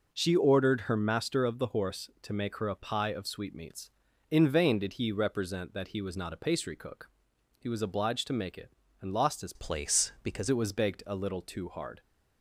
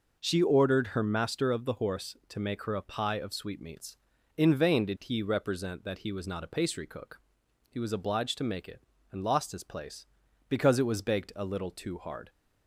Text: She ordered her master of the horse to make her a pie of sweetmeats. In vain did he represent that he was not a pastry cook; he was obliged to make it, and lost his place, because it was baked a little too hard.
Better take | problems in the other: second | changes voice from "place" to "because"; from 9.5 to 10.4 s; 0.9 s long

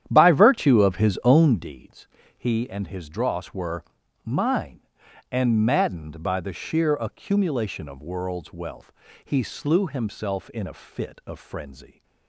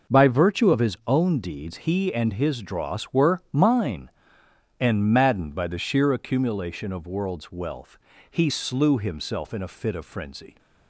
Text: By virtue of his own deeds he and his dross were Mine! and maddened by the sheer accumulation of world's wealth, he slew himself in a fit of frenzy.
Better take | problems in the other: second | starts louder than the rest; strong; until 1.7 s; 10.5 dB // pauses between "deeds" and "he"; slight; at 2.0 s; 0.28 s long // pauses between "were" and "Mine"; at 3.8 s; 0.40 s long

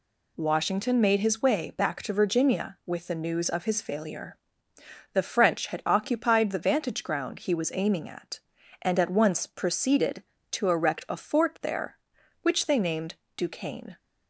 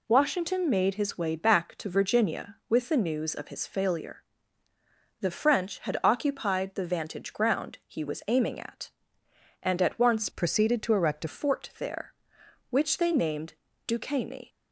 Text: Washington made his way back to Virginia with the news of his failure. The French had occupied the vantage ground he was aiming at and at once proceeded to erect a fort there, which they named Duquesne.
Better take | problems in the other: first | changes voice from "proceeded" to "a"; from 10.3 to 11.2 s; 0.9 s long // pauses between "named" and "Duquesne"; slight; at 13.5 s; 0.32 s long; slight in the first

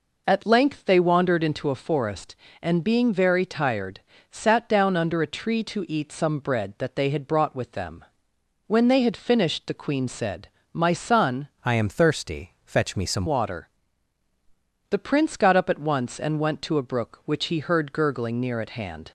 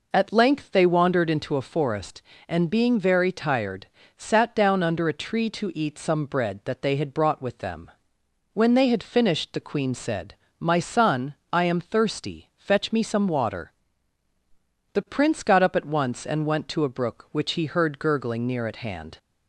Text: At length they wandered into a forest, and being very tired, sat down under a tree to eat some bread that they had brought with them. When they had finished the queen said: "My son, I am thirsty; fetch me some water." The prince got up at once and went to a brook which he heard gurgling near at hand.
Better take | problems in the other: second | changes voice from "I" to "some"; from 11.6 to 13.2 s; 1.6 s long

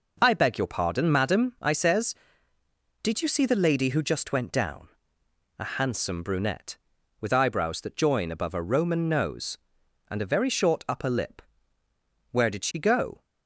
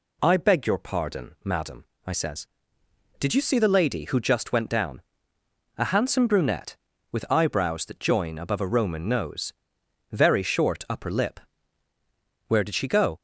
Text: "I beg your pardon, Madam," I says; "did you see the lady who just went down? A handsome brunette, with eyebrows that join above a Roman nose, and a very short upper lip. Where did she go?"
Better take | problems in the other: first | skips "and a"; at 9.8 s

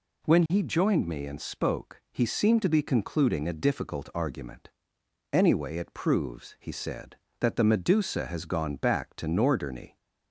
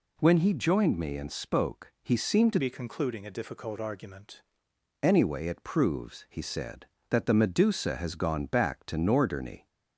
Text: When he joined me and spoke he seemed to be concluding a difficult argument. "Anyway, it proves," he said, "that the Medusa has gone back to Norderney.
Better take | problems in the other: first | changes voice from "be" to "argument"; from 2.5 to 4.3 s; 1.8 s long

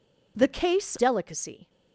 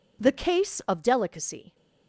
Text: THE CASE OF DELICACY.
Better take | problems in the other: second | skips "OF"; at 0.9 s

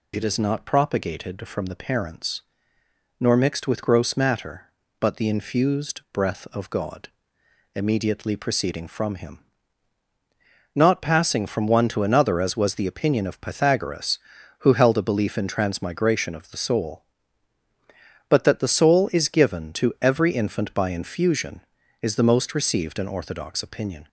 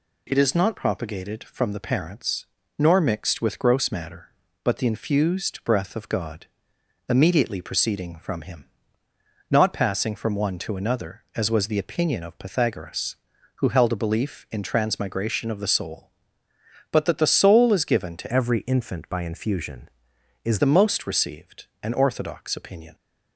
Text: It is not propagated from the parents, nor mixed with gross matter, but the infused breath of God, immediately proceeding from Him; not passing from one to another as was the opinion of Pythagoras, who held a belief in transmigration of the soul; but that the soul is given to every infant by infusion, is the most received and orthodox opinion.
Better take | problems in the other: first | changes voice from "every" to "is"; from 18.3 to 20.5 s; 2.2 s long

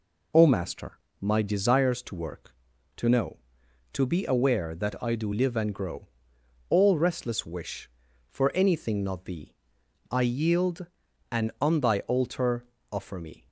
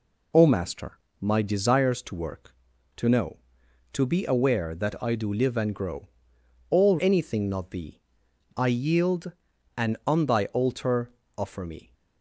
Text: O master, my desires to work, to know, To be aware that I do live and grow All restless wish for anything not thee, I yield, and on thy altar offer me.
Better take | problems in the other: first | pauses between "grow" and "All"; noticeable; at 6.0 s; 0.62 s long; noticeable in the first // skips "restless wish for"; at 6.9 s // pauses between "altar" and "offer"; slight; at 11.1 s; 0.26 s long; slight in the first

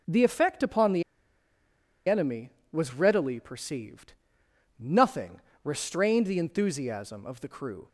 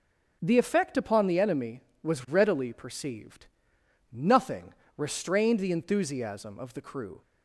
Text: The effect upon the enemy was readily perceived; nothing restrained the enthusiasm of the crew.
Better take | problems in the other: second | pauses between "the" and "enemy"; at 1.0 s; 1.0 s long // pauses between "nothing" and "restrained"; slight; at 5.4 s; 0.24 s long; slight in the second

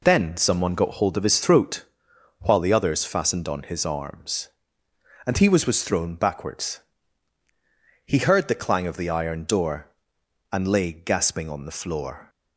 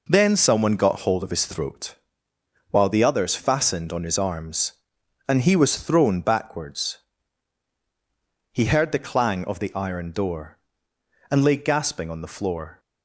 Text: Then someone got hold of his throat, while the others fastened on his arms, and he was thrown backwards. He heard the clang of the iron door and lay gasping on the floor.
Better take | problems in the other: second | says "was" twice; at 5.6 s

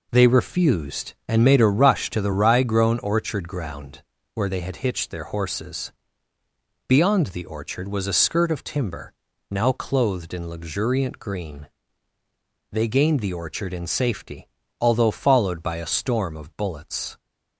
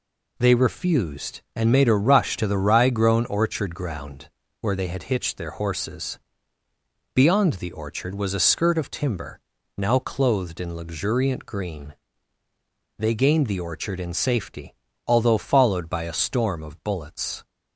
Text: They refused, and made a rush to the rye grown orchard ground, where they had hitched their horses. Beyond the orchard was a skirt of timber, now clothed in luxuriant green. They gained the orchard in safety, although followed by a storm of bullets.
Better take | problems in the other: second | starts louder than the rest; until 2.0 s; 4 dB

